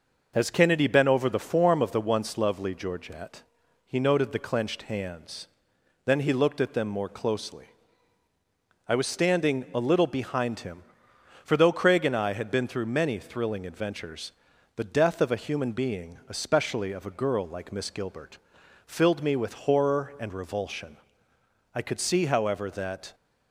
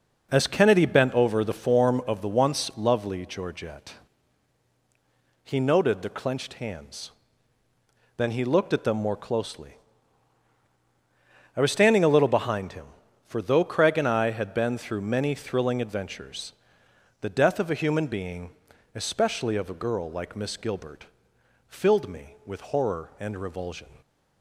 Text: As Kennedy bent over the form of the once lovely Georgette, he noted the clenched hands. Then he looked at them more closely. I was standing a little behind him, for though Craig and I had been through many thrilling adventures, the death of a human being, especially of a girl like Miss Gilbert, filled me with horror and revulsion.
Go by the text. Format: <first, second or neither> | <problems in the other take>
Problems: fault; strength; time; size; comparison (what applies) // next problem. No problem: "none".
second | goes on to say "I could see however that"; from 21.7 s on; 1.3 s long